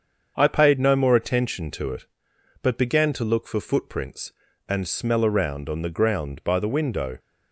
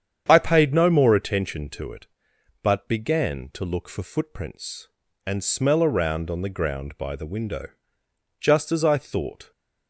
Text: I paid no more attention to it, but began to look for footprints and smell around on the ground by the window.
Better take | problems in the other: first | starts louder than the rest; strong; until 1.2 s; 8.5 dB; also in the first // goes on to say "Just as I thought"; noticeable; from 8.4 s on; 1.1 s long

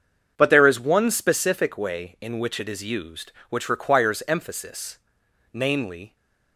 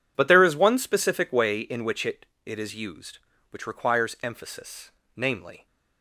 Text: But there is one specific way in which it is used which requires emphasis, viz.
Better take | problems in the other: first | says "it" twice; at 2.4 s

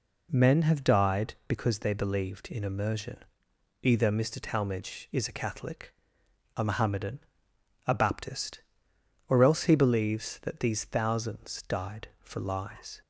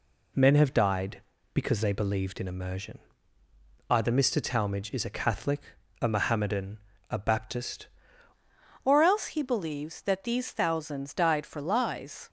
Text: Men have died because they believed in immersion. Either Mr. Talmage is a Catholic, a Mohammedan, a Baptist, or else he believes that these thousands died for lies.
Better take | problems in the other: first | changes voice at "or"; from 8.8 s on; 3.4 s long

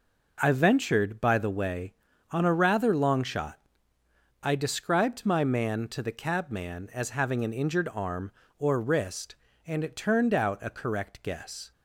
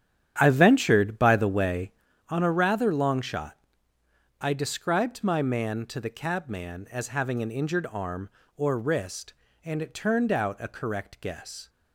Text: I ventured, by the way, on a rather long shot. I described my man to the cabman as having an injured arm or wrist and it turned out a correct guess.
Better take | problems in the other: first | starts louder than the rest; strong; until 2.1 s; 10 dB

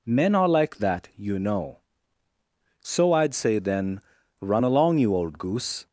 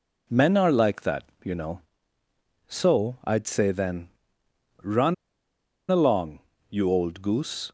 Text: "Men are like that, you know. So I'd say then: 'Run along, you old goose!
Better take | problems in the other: first | pauses between "Run" and "along"; noticeable; at 5.1 s; 0.76 s long

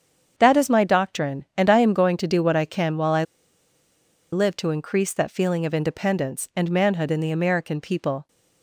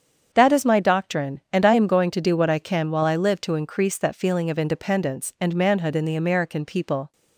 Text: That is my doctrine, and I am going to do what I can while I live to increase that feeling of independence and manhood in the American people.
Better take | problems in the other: second | starts louder than the rest; strong; until 1.3 s; 7.5 dB; strong in the second // pauses between "I" and "live"; at 3.2 s; 1.1 s long

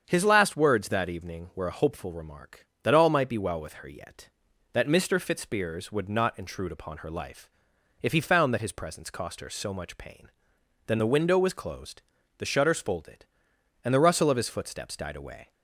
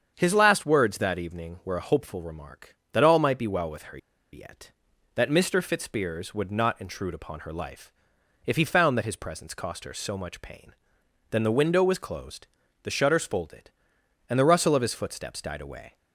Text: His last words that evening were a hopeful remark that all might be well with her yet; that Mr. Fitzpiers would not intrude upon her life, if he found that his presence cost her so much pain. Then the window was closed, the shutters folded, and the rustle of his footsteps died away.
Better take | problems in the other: first | starts louder than the rest; strong; until 1.1 s; 7.5 dB; strong in the first // pauses between "her" and "yet"; slight; at 3.9 s; 0.34 s long

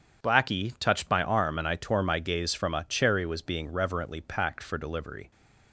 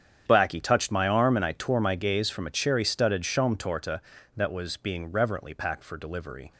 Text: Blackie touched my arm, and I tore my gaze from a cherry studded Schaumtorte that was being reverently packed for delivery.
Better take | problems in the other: second | starts louder than the rest; strong; until 1.2 s; 8 dB; strong in the second // skips "studded Schaumtorte that"; at 3.2 s

